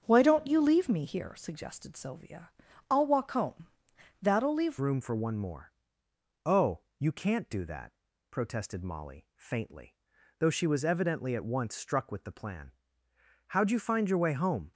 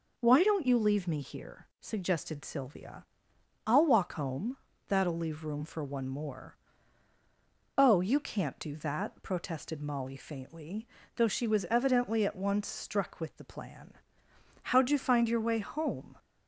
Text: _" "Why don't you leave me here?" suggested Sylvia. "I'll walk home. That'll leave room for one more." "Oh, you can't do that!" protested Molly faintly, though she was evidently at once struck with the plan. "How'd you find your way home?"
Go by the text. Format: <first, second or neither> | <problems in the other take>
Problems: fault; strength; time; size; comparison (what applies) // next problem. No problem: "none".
second | starts louder than the rest; strong; until 1.0 s; 7.5 dB // changes voice at "room"; from 4.8 s on; 9.9 s long